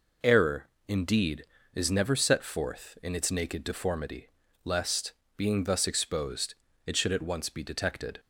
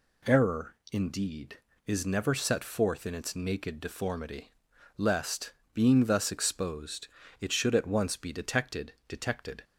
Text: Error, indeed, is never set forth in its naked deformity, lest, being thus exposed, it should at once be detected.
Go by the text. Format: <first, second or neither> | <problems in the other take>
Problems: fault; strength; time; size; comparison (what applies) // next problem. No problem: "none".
first | says "detected" twice; at 9.0 s